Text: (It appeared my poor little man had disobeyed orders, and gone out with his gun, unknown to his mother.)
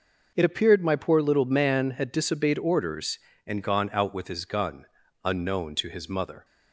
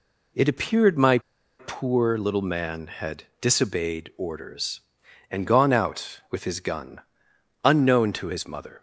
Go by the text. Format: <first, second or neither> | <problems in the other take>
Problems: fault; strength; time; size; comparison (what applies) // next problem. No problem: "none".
first | pauses between "my" and "poor"; at 1.1 s; 0.40 s long // pauses between "had" and "disobeyed"; slight; at 3.2 s; 0.16 s long